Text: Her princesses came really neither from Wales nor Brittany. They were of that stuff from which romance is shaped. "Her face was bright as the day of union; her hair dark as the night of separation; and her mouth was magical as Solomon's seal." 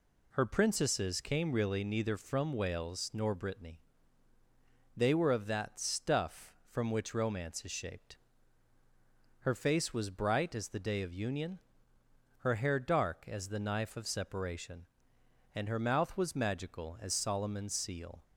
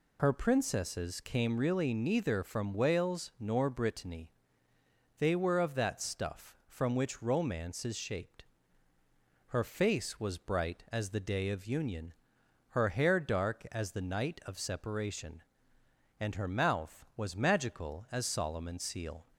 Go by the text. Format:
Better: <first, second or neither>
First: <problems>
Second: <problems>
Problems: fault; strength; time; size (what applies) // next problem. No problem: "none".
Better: second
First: says "knife" for "night"; at 13.5 s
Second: none